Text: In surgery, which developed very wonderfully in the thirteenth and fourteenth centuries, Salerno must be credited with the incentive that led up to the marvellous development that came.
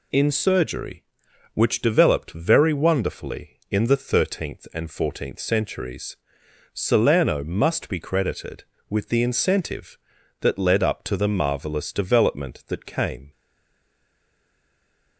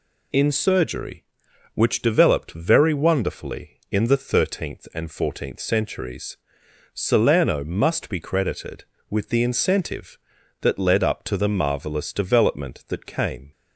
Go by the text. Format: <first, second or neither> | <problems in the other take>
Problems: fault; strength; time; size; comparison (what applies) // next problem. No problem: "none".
second | stays silent after the last word; noticeable; from 13.3 s on; 1.8 s long